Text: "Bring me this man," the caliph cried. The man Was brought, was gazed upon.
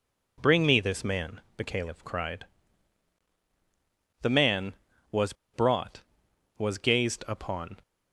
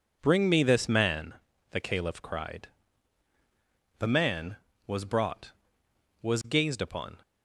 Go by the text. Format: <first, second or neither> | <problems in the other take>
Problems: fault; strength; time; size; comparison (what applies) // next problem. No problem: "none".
second | pauses between "Was" and "brought"; slight; at 5.3 s; 0.20 s long